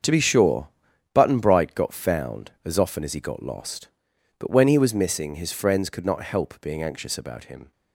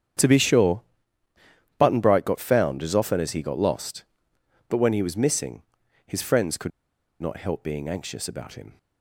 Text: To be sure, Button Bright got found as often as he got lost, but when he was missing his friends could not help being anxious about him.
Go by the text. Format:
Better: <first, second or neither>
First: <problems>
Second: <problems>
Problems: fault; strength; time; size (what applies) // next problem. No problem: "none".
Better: first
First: starts louder than the rest; until 1.4 s; 6.5 dB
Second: starts louder than the rest; strong; until 2.1 s; 8.5 dB // pauses between "missing" and "his"; noticeable; at 5.6 s; 0.46 s long // pauses between "could" and "not"; noticeable; at 6.7 s; 0.51 s long